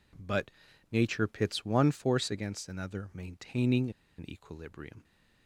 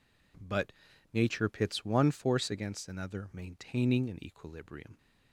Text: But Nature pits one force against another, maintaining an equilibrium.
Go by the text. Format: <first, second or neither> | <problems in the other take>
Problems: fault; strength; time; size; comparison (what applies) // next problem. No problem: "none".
second | pauses between "But" and "Nature"; at 0.4 s; 0.42 s long; also in the second // pauses between "maintaining" and "an"; slight; at 3.8 s; 0.28 s long